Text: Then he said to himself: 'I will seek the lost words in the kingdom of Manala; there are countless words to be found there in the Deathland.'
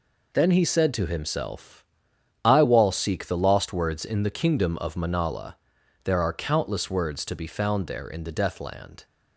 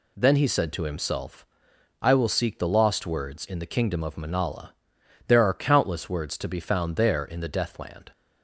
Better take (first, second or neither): second